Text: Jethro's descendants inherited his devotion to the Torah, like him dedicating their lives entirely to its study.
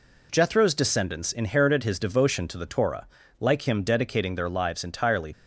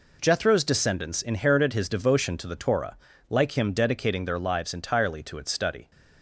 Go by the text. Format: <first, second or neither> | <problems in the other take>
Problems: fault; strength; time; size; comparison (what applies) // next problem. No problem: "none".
second | stops before "to its study"; at 5.3 s